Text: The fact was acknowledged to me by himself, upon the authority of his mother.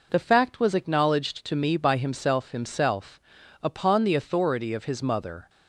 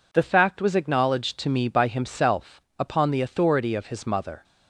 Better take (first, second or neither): second